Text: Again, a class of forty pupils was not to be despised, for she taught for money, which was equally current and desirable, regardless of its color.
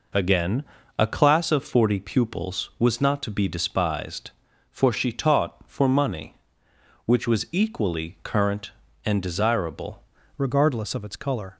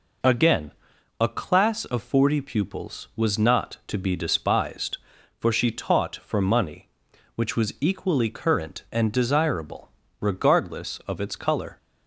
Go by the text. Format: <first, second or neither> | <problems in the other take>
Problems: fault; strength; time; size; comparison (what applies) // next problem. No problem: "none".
second | changes voice at "regardless"; from 10.3 s on; 1.2 s long